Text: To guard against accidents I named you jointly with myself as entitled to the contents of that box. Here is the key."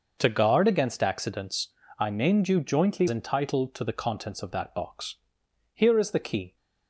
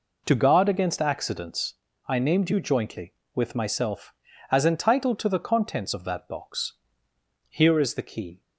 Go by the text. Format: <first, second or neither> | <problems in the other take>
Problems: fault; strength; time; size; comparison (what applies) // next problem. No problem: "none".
second | pauses between "accidents" and "I"; slight; at 1.6 s; 0.32 s long; slight in the second // skips "with myself as"; at 3.0 s